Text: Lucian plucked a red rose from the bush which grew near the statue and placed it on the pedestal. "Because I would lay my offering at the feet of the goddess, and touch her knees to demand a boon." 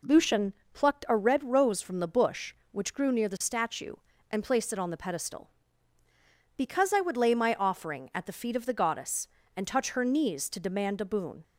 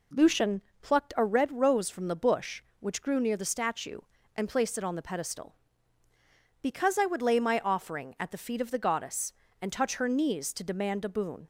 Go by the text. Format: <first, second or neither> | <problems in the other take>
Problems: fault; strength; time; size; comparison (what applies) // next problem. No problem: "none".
neither | pauses between "Lucian" and "plucked"; slight; the same in both